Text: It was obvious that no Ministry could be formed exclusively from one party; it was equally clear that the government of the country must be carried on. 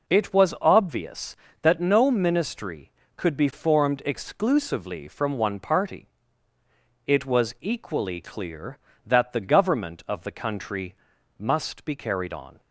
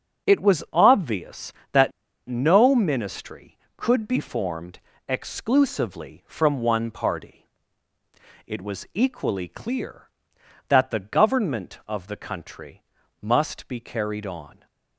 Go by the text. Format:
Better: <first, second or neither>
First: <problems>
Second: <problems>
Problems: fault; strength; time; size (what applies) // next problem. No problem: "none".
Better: first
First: pauses between "country" and "must"; at 10.9 s; 0.42 s long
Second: starts louder than the rest; strong; until 1.3 s; 7.5 dB // pauses between "that" and "no"; at 1.9 s; 0.36 s long // pauses between "formed" and "exclusively"; slight; at 4.7 s; 0.30 s long // pauses between "country" and "must"; at 12.8 s; 0.40 s long